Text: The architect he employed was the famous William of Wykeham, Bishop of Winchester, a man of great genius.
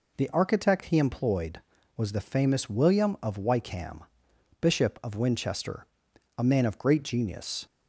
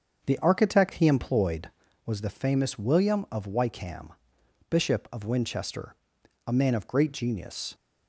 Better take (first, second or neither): first